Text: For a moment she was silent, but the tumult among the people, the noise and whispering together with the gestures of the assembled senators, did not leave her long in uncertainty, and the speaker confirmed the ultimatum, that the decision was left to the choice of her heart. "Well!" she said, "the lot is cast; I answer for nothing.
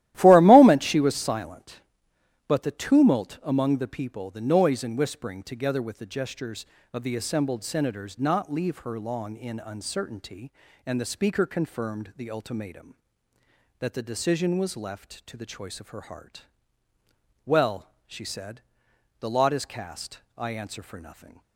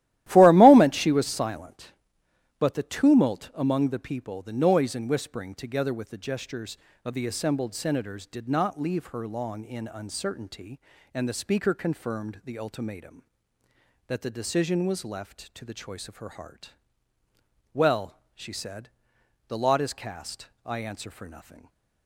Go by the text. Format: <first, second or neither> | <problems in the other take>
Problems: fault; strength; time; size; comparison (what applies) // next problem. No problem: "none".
second | starts louder than the rest; strong; until 1.1 s; 14 dB; strong in the second // skips "did"; at 8.1 s